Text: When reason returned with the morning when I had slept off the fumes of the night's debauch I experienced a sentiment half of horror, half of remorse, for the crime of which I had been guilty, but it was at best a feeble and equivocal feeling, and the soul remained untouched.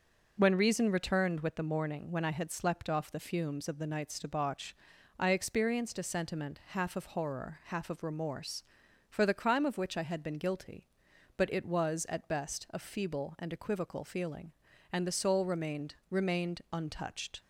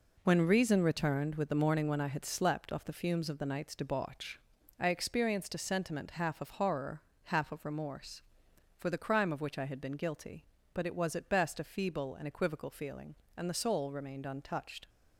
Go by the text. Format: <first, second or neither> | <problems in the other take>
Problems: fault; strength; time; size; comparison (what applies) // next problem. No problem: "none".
second | pauses between "debauch" and "I"; noticeable; at 4.7 s; 0.46 s long; also in the second // says "remained" twice; at 16.0 s